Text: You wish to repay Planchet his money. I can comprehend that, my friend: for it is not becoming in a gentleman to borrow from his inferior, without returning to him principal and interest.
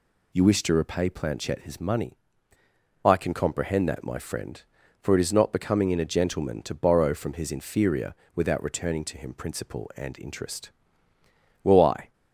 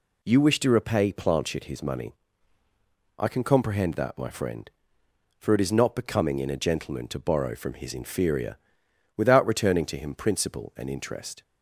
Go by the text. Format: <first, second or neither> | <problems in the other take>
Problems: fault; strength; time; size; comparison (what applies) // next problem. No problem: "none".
second | goes on to say "Well I"; from 11.6 s on; 0.50 s long